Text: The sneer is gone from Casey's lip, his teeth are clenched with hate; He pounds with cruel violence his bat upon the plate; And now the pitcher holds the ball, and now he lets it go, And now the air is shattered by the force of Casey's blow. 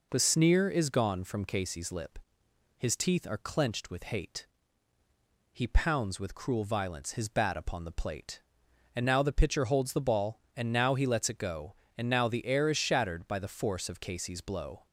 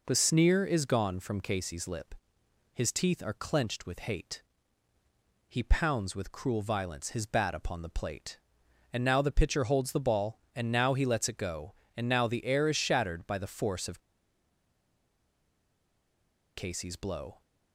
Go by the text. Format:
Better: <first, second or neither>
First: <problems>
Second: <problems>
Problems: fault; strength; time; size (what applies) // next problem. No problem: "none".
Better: first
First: none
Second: pauses between "of" and "Casey's"; strong; at 13.9 s; 2.5 s long